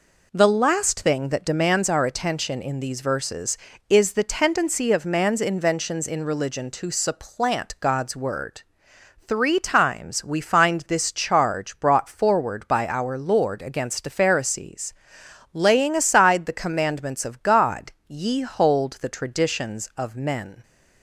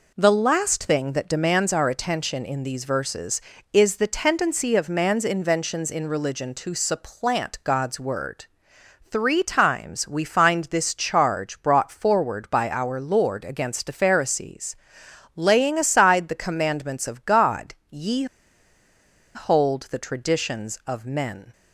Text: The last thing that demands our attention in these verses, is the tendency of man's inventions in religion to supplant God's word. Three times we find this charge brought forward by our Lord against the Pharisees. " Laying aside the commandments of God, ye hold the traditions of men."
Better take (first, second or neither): first